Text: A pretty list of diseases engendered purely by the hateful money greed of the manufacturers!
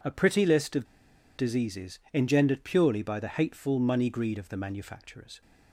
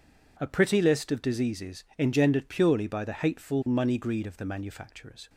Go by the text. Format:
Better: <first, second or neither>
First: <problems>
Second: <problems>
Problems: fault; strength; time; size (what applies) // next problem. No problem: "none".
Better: second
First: pauses between "of" and "diseases"; noticeable; at 0.8 s; 0.53 s long // pauses between "diseases" and "engendered"; slight; at 1.9 s; 0.16 s long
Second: pauses between "diseases" and "engendered"; slight; at 1.8 s; 0.16 s long